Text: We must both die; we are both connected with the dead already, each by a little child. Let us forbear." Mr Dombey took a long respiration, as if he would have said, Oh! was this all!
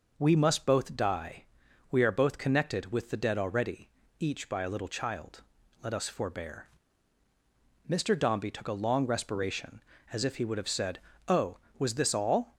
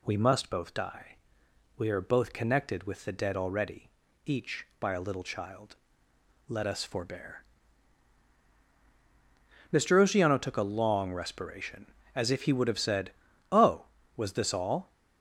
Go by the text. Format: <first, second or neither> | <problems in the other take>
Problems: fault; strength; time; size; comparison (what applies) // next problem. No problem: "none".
first | says "Oceano" for "Dombey"; at 10.0 s